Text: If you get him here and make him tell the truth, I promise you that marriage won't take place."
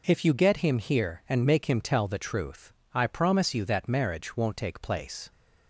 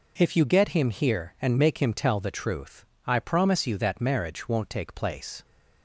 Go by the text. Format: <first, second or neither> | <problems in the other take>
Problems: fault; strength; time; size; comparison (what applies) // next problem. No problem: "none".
neither | none